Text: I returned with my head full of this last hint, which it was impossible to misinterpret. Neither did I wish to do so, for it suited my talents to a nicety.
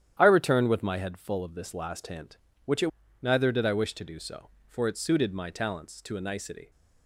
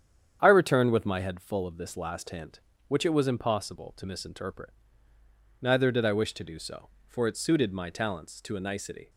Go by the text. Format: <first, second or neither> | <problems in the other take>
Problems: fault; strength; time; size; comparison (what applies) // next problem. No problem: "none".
second | starts louder than the rest; strong; until 1.1 s; 10.5 dB; strong in the second // skips "was impossible to misinterpret"; at 3.0 s